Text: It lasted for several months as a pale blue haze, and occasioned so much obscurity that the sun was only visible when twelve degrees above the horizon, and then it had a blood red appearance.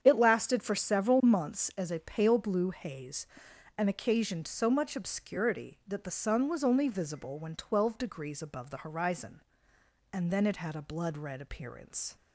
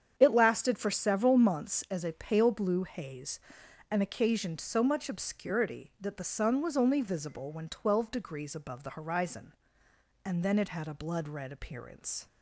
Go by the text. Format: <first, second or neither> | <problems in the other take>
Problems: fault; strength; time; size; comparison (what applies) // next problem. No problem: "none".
neither | starts louder than the rest; strong; the same in both